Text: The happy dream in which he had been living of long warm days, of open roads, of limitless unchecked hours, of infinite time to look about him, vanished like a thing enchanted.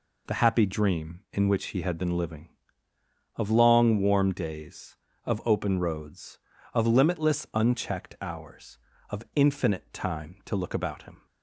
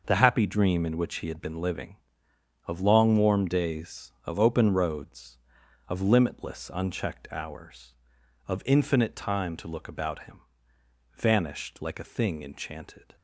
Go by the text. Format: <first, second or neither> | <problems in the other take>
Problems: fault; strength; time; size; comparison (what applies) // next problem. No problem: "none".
second | stops before "vanished like a thing enchanted"; at 11.2 s